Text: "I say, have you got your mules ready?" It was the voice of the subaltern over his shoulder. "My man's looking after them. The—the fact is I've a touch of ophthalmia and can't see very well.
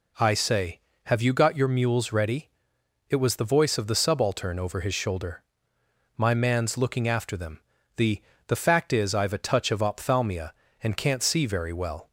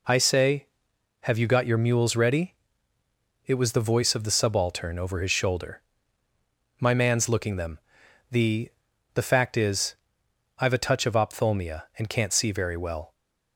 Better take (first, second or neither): first